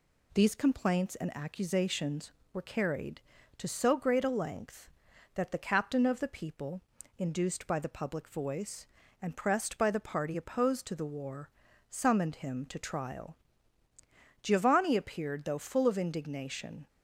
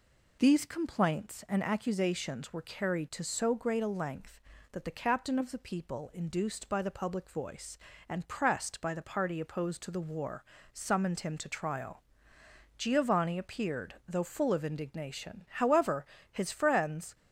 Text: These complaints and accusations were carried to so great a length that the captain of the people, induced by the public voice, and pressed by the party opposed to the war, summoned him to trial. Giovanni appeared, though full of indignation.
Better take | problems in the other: first | goes on to say "However his friends"; strong; from 15.4 s on; 1.6 s long

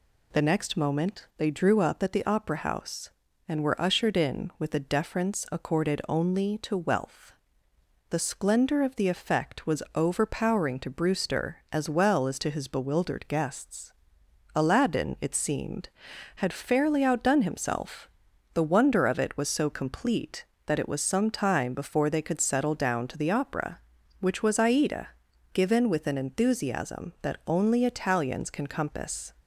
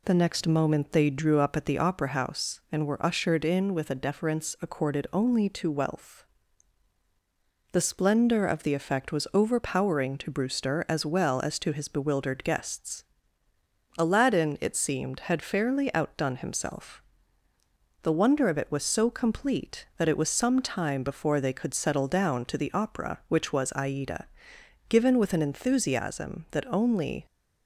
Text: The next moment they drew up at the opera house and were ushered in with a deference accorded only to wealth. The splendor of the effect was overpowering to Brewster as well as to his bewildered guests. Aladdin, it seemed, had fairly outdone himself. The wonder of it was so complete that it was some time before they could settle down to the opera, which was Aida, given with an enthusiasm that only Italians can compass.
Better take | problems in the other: first | stops before "Italians can compass"; at 27.2 s

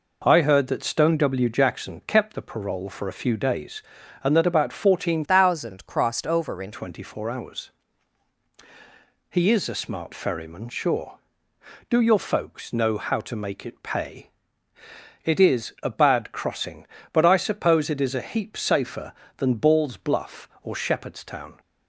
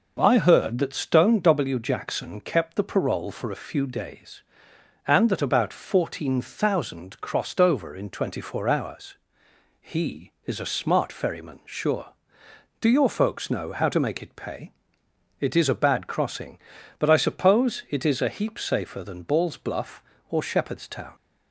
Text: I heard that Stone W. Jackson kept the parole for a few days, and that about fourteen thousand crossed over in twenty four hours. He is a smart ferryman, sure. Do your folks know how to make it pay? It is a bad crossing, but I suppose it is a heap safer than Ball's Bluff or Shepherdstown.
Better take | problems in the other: second | changes voice from "thousand" to "in"; from 5.2 to 6.7 s; 1.5 s long

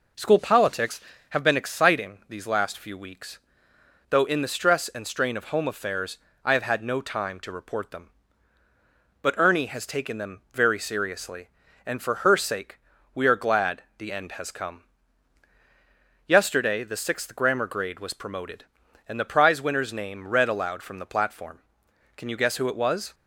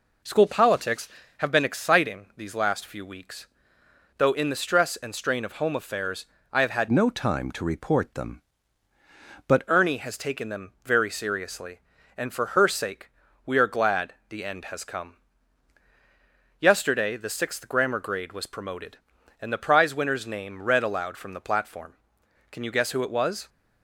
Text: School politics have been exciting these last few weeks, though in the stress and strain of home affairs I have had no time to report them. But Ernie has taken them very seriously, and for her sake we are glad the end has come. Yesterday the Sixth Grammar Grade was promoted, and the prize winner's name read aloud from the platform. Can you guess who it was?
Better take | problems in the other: first | pauses between "affairs" and "I"; slight; at 6.2 s; 0.28 s long; slight in the first // changes voice from "no" to "But"; from 6.9 to 9.6 s; 2.7 s long // pauses between "sake" and "we"; slight; at 13.0 s; 0.36 s long; slight in the first

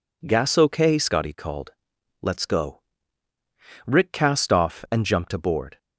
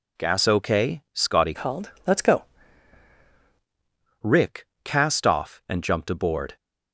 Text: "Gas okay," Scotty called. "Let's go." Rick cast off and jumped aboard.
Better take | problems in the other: first | changes voice from "called" to "go"; from 1.5 to 2.4 s; 0.9 s long // pauses between "Rick" and "cast"; slight; at 4.6 s; 0.18 s long

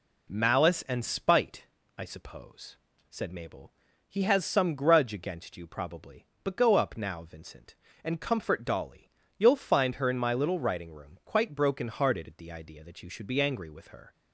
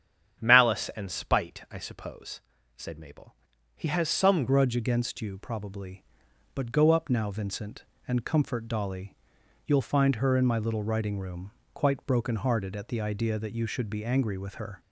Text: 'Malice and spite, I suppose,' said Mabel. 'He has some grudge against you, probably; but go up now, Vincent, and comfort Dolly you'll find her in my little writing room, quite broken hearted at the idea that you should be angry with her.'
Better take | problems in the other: first | starts louder than the rest; strong; until 1.4 s; 9 dB // changes voice at "grudge"; from 4.4 s on; 10.3 s long // pauses between "Dolly" and "you'll"; noticeable; at 9.1 s; 0.50 s long; slight in the first

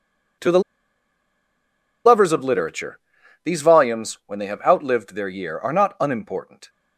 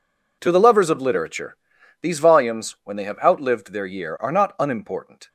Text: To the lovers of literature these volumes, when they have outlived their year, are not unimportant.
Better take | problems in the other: second | pauses between "the" and "lovers"; strong; at 0.6 s; 1.4 s long // pauses between "literature" and "these"; at 2.9 s; 0.44 s long; also in the second

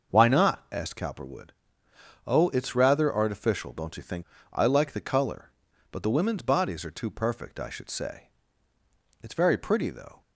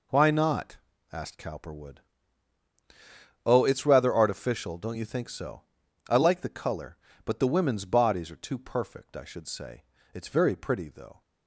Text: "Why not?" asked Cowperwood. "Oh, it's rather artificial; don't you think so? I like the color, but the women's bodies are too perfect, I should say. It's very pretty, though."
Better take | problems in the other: second | starts louder than the rest; noticeable; until 1.1 s; 6 dB // skips "so"; at 4.3 s

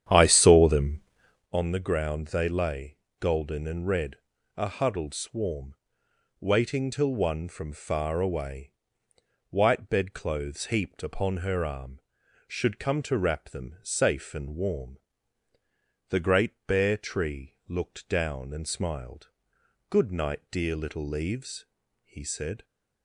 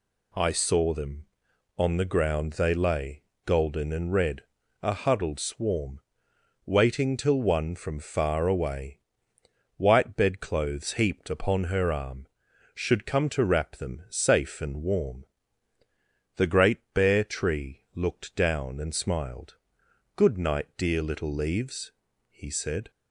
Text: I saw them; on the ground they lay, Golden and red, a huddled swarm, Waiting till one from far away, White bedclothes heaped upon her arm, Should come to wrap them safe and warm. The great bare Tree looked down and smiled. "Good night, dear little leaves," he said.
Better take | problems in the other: second | starts louder than the rest; strong; until 1.5 s; 9.5 dB // pauses between "great" and "bare"; slight; at 16.5 s; 0.16 s long; slight in the second

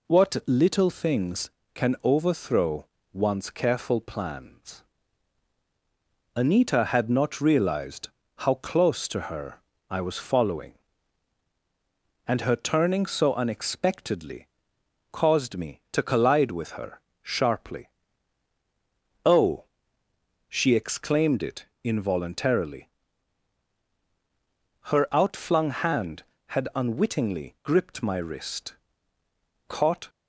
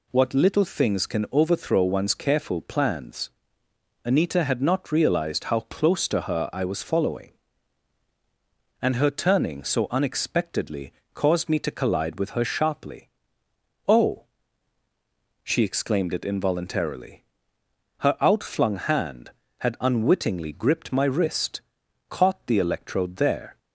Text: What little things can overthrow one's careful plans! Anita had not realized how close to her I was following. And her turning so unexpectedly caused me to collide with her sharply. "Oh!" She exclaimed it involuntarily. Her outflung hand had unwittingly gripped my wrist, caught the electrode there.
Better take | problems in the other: second | pauses between "overthrow" and "one's"; slight; at 2.8 s; 0.26 s long // pauses between "realized" and "how"; slight; at 8.0 s; 0.28 s long // pauses between "her" and "I"; slight; at 9.5 s; 0.30 s long // pauses between "unexpectedly" and "caused"; noticeable; at 14.4 s; 0.64 s long; slight in the second // pauses between "her" and "sharply"; slight; at 16.9 s; 0.22 s long // pauses between "it" and "involuntarily"; slight; at 21.6 s; 0.18 s long // stops before "the electrode there"; at 30.0 s

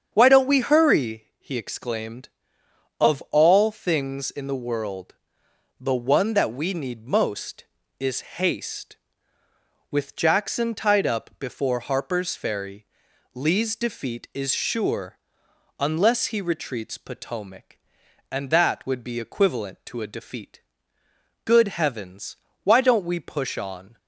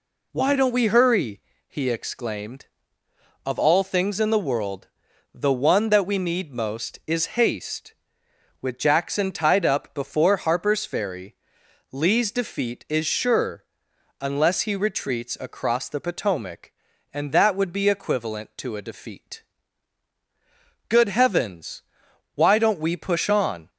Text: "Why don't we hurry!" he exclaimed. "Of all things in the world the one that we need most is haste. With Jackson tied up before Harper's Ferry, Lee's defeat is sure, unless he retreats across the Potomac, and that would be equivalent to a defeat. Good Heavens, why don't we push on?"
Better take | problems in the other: second | starts louder than the rest; strong; until 1.1 s; 7.5 dB // pauses between "world" and "the"; noticeable; at 5.1 s; 0.64 s long; noticeable in the second // skips "across the"; at 16.9 s

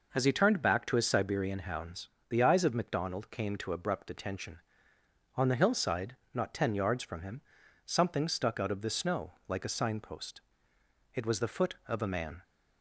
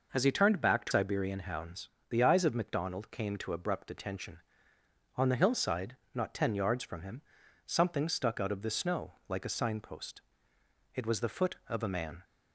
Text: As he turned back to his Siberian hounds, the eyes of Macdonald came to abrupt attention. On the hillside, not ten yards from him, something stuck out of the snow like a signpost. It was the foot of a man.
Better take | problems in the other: first | skips "his"; at 0.9 s

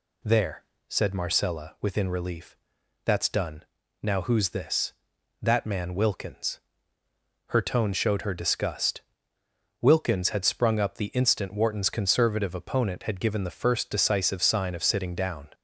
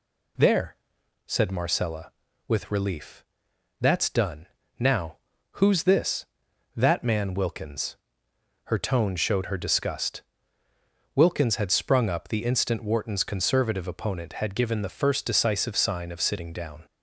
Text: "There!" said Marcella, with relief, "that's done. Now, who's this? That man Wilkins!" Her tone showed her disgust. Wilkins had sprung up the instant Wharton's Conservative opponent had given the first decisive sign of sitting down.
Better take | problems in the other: second | says "within" for "with"; at 1.7 s

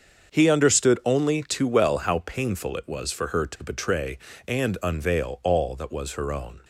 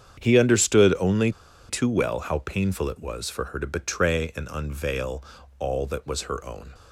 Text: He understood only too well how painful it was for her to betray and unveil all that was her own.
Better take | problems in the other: first | starts louder than the rest; strong; until 1.2 s; 8 dB; also in the first // pauses between "only" and "too"; at 1.3 s; 0.38 s long // pauses between "unveil" and "all"; slight; at 5.2 s; 0.34 s long

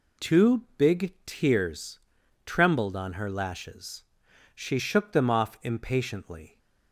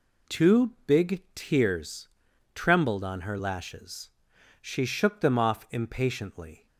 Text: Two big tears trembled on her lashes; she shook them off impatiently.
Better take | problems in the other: neither | pauses between "tears" and "trembled"; the same in both

